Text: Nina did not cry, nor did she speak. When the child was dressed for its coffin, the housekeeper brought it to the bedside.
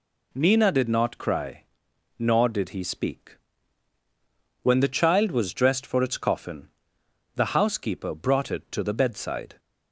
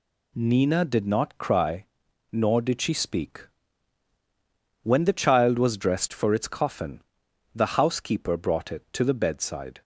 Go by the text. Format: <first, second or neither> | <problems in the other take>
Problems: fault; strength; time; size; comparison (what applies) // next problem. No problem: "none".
second | says "he" for "she"; at 2.6 s